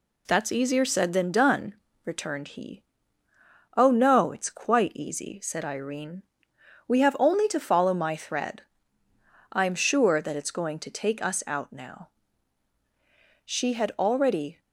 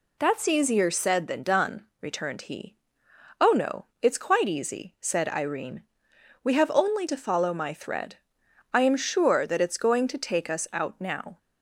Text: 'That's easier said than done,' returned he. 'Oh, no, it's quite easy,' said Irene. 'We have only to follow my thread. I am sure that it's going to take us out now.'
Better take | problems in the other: second | goes on to say "She had already"; noticeable; from 13.4 s on; 1.1 s long

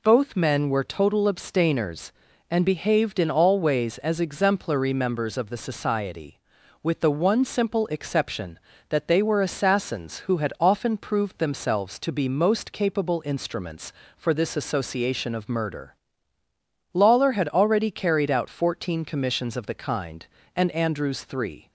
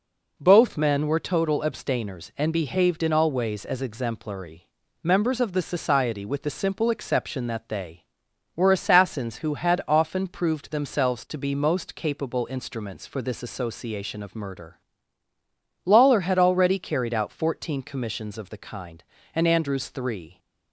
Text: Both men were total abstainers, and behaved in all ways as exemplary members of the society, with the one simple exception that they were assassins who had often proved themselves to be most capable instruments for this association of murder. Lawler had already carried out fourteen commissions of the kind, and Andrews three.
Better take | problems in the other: first | pauses between "exemplary" and "members"; at 4.6 s; 0.38 s long // skips "one"; at 6.5 s

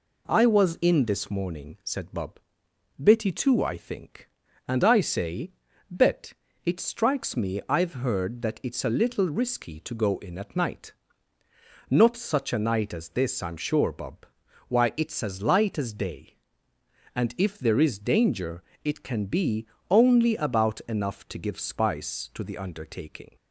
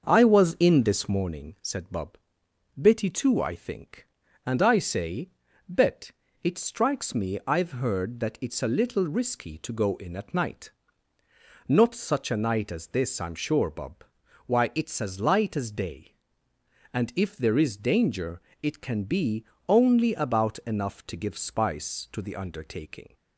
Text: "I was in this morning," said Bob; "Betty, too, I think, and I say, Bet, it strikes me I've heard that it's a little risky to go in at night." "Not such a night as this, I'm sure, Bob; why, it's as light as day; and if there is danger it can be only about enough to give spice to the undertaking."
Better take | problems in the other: first | starts louder than the rest; until 1.4 s; 6.5 dB // pauses between "danger" and "it"; slight; at 18.4 s; 0.20 s long; slight in the first // pauses between "be" and "only"; slight; at 19.4 s; 0.24 s long; slight in the first

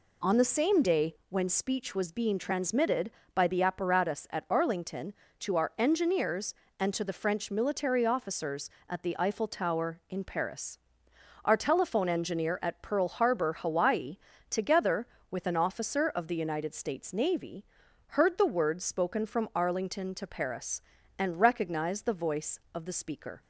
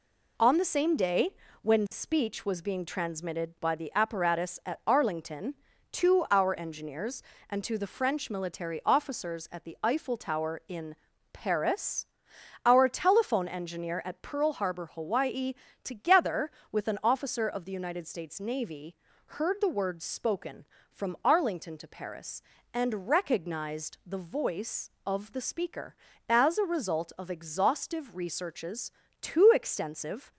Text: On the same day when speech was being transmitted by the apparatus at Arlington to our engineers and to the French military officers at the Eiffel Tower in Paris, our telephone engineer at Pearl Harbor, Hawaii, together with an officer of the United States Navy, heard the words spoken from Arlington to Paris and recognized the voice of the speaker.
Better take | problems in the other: first | pauses between "day" and "when"; slight; at 1.3 s; 0.28 s long // pauses between "in" and "Paris"; at 10.9 s; 0.38 s long // goes on to say "As a result of exhaustive researches too extensive"; strong; from 26.2 s on; 4.0 s long

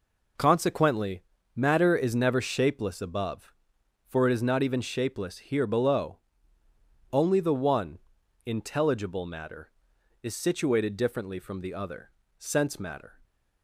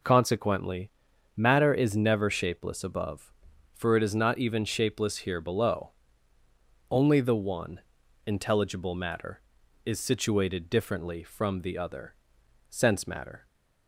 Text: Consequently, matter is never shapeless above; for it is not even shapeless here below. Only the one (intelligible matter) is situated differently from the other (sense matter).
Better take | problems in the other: neither | none

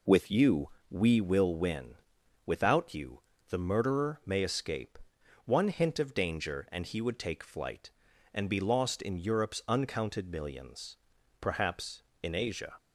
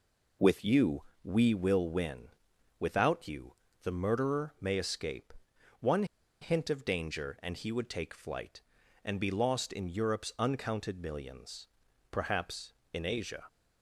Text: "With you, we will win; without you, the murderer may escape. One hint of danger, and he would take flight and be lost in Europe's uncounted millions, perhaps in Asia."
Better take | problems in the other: first | pauses between "One" and "hint"; at 6.0 s; 0.37 s long

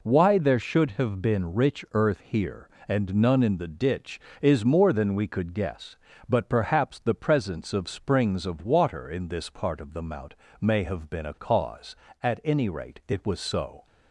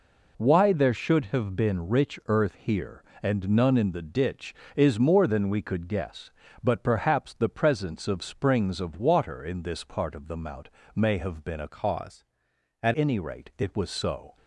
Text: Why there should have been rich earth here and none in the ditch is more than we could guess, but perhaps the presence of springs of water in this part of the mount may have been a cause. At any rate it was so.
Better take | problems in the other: first | pauses between "mount" and "may"; slight; at 10.6 s; 0.26 s long; slight in the first // changes voice from "cause" to "At"; from 11.6 to 12.9 s; 1.3 s long

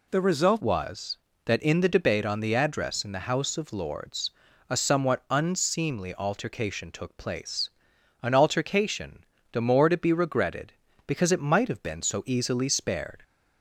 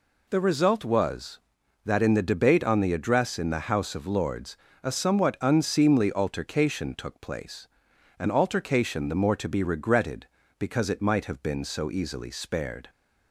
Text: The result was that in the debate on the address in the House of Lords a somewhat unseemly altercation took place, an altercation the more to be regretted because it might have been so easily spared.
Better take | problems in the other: second | changes voice at "was"; from 0.6 s on; 12.6 s long // pauses between "Lords" and "a"; at 4.2 s; 0.40 s long; slight in the second // pauses between "altercation" and "the"; slight; at 9.2 s; 0.30 s long

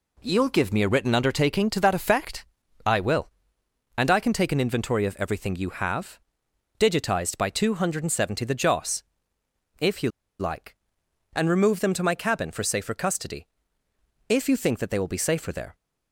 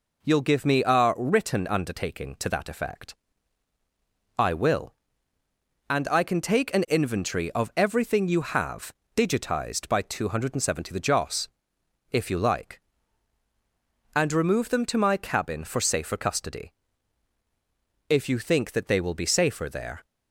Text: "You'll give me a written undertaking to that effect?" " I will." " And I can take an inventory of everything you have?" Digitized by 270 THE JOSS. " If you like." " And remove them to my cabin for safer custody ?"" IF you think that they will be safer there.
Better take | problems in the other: second | pauses between "you" and "like"; slight; at 10.0 s; 0.29 s long

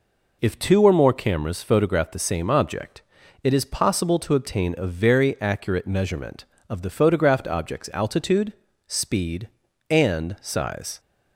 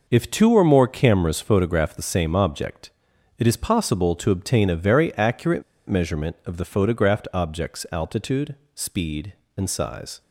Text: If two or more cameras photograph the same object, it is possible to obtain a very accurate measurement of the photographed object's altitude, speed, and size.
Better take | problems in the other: first | pauses between "accurate" and "measurement"; slight; at 5.6 s; 0.26 s long

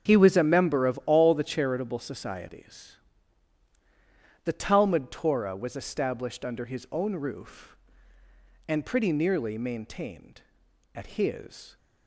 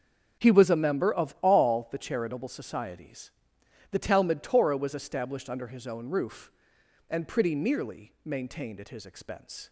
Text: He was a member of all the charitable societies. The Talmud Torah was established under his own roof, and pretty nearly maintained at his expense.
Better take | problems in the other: second | starts louder than the rest; until 1.1 s; 7 dB; also in the second // stops before "expense"; at 11.7 s

